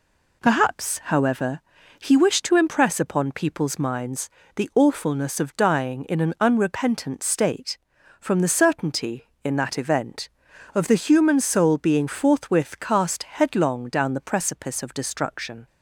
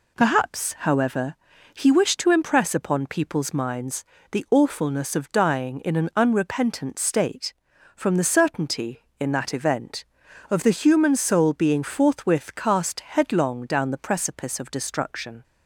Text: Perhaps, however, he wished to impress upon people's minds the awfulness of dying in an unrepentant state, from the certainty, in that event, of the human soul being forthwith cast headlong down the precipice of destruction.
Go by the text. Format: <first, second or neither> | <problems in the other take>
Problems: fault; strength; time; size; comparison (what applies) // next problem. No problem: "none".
neither | pauses between "minds" and "the"; slight; the same in both